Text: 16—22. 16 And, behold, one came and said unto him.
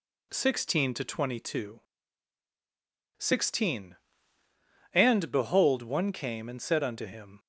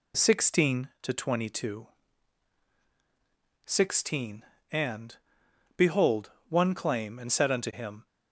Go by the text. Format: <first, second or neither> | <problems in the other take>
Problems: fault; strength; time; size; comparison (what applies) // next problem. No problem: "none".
first | says "claim" for "came"; at 6.7 s